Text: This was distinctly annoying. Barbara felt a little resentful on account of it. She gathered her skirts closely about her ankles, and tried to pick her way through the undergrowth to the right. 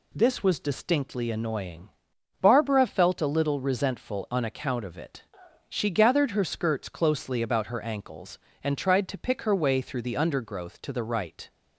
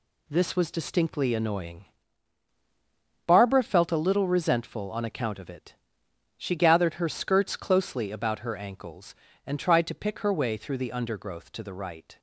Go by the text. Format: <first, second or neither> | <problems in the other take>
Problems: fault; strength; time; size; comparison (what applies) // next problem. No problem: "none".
first | gets quieter; throughout; 6.5 dB